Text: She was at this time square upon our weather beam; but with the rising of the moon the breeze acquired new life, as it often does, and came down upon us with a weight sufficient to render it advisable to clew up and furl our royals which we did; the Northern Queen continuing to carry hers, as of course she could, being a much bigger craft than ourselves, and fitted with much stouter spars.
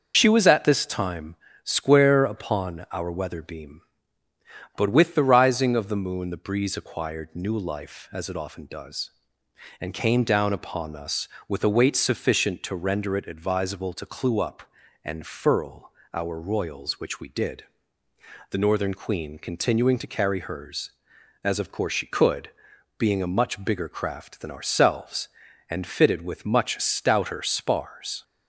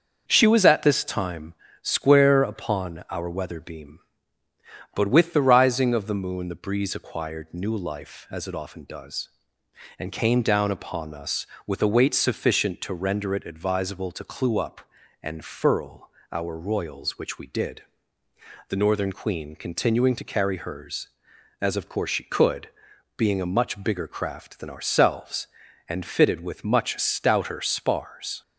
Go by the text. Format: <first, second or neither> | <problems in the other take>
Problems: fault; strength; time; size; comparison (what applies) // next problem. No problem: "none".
second | loses the start of "She"; at 0.1 s; 65 ms // starts louder than the rest; until 1.1 s; 6.5 dB; also in the second // pauses between "time" and "square"; slight; at 1.3 s; 0.30 s long; slight in the second // pauses between "furl" and "our"; slight; at 15.9 s; 0.24 s long; slight in the second